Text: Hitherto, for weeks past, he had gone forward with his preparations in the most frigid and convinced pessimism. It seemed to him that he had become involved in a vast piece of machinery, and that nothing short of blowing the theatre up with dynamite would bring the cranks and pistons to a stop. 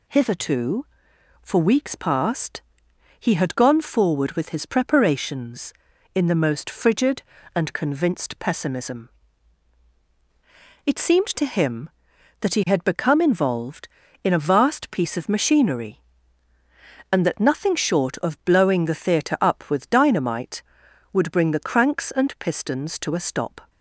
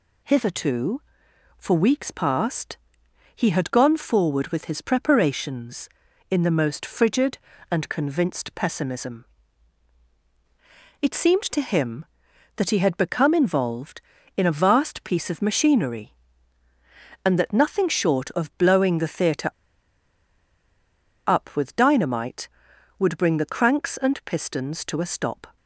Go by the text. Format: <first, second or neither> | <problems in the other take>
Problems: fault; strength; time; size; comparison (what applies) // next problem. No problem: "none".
first | pauses between "theatre" and "up"; strong; at 19.5 s; 1.7 s long